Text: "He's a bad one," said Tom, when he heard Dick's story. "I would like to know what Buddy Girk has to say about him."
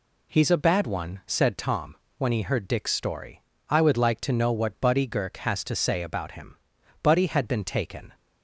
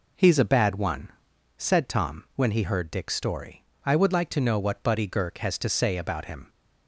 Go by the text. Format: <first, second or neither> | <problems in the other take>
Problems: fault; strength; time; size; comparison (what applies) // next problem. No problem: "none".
second | goes on to say "Buddy had been taken"; noticeable; from 7.0 s on; 1.1 s long